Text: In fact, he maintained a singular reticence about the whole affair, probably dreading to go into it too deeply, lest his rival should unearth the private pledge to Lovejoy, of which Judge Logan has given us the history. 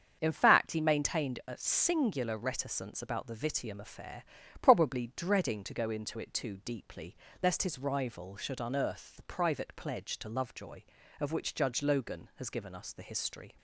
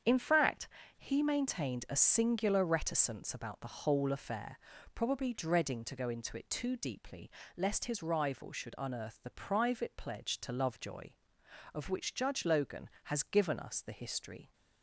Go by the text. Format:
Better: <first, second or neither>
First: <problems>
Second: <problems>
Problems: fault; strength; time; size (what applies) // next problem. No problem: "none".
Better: second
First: starts louder than the rest; until 1.2 s; 7 dB // says "vitium" for "whole"; at 3.3 s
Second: starts louder than the rest; strong; until 1.3 s; 7.5 dB